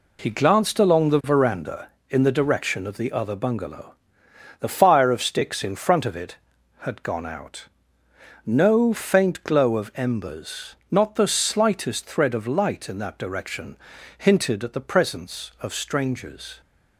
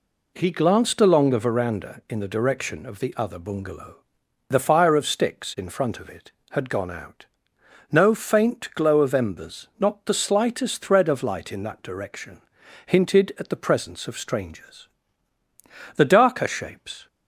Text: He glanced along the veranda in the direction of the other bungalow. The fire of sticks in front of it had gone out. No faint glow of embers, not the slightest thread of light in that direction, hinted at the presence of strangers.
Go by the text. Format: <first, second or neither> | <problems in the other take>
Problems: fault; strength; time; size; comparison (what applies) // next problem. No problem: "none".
first | goes on to say "The darker shapes"; noticeable; from 15.9 s on; 1.1 s long